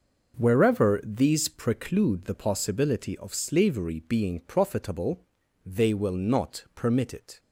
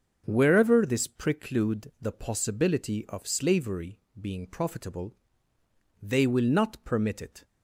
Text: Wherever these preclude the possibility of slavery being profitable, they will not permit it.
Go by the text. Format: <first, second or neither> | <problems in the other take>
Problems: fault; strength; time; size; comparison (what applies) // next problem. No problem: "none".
first | starts louder than the rest; until 1.2 s; 6.5 dB // says "this" for "these"; at 0.8 s // pauses between "slavery" and "being"; slight; at 3.9 s; 0.20 s long